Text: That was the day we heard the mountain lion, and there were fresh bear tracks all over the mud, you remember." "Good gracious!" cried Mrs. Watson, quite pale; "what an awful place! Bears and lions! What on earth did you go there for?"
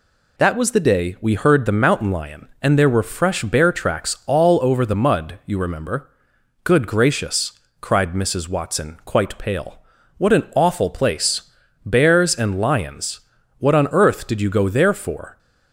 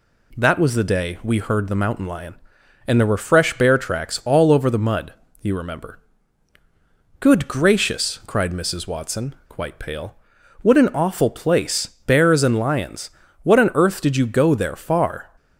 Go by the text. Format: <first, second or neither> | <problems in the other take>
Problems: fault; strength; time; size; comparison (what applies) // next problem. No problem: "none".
first | says "far" for "for"; at 14.7 s